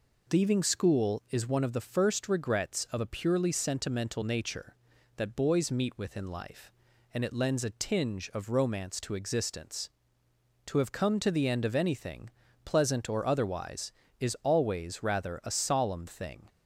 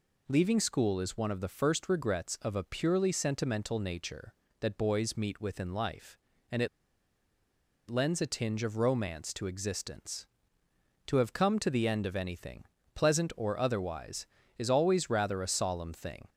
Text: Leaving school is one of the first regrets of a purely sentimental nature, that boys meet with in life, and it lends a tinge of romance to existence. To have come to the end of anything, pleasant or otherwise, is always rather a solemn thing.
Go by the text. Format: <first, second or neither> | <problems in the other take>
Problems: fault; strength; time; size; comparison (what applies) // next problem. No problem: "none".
first | pauses between "it" and "lends"; at 6.6 s; 1.2 s long